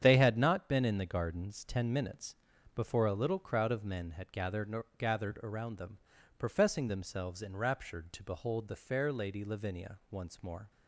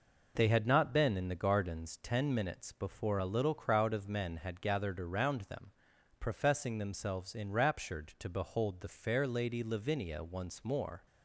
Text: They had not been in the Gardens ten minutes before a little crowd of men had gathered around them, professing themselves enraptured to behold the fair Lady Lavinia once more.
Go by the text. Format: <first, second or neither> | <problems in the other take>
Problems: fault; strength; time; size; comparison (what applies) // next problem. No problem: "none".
second | starts louder than the rest; strong; until 1.0 s; 8.5 dB // pauses between "minutes" and "before"; at 2.3 s; 0.40 s long // says "gathered" twice; at 4.9 s